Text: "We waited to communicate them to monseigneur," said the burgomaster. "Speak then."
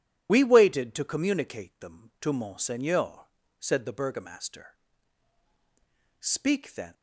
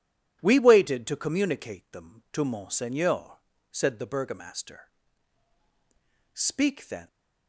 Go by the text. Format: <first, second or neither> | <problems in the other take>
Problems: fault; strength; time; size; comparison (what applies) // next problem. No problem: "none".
second | loses the start of "We"; at 0.2 s; 45 ms